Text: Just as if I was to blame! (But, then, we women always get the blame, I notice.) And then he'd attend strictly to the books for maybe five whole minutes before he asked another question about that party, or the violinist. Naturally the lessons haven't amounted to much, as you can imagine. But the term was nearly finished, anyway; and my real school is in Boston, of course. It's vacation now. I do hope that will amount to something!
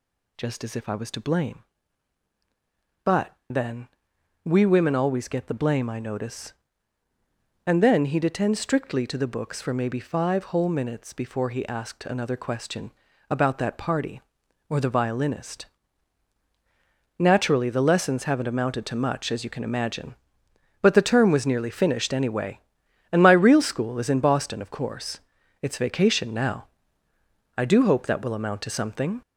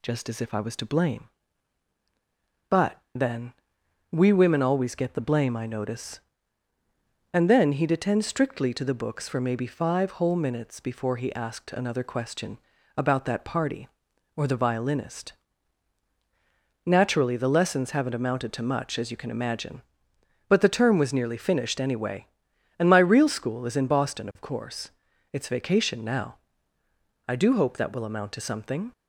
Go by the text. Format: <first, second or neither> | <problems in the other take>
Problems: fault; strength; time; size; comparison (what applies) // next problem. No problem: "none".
second | gets louder; noticeable; throughout; 5 dB // pauses between "question" and "about"; at 12.9 s; 0.38 s long; also in the second